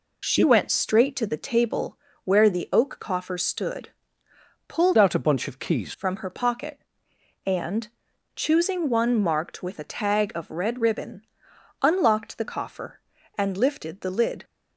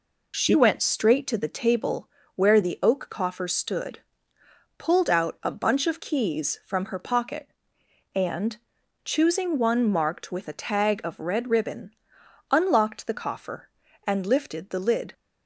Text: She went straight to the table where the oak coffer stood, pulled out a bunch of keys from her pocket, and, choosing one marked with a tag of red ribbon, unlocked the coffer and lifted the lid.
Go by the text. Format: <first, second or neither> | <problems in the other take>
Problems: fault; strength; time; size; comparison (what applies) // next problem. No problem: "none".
second | pauses between "table" and "where"; slight; at 1.9 s; 0.26 s long; slight in the second // changes voice from "out" to "keys"; from 4.9 to 5.9 s; 1.0 s long